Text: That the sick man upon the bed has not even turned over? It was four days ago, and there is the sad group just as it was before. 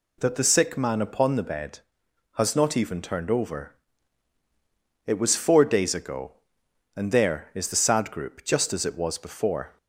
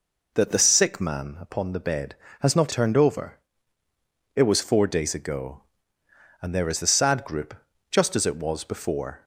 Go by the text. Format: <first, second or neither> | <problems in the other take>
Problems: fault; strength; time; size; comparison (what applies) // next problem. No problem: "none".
first | skips "even"; at 2.7 s // pauses between "group" and "just"; slight; at 7.5 s; 0.36 s long